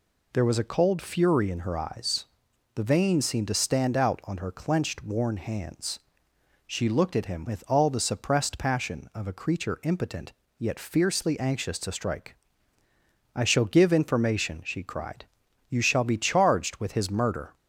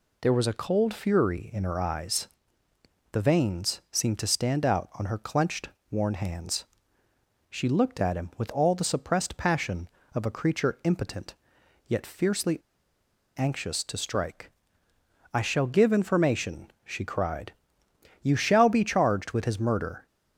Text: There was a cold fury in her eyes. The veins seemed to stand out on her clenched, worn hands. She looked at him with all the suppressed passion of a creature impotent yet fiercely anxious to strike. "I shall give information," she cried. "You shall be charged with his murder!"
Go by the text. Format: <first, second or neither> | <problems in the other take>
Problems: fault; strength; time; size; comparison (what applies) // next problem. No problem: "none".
first | pauses between "impotent" and "yet"; noticeable; at 11.3 s; 0.52 s long; slight in the first // pauses between "fiercely" and "anxious"; noticeable; at 12.5 s; 0.78 s long